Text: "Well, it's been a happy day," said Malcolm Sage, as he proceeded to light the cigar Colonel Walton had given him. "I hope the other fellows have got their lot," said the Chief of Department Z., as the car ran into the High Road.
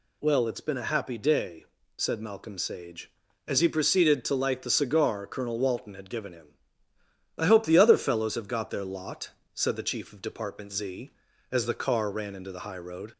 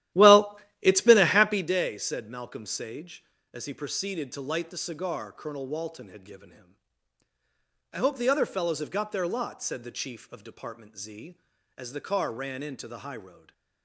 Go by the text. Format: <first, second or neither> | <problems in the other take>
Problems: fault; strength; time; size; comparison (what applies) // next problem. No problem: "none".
first | starts louder than the rest; strong; until 1.7 s; 13.5 dB // stays silent after the last word; slight; from 13.3 s on; 0.5 s long